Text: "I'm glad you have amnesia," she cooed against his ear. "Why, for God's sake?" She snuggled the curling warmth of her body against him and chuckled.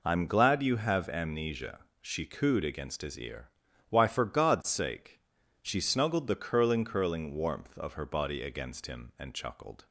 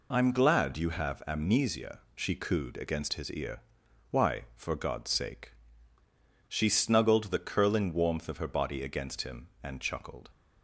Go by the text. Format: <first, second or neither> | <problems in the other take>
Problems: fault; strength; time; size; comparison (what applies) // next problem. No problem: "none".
second | says "curling" twice; at 6.8 s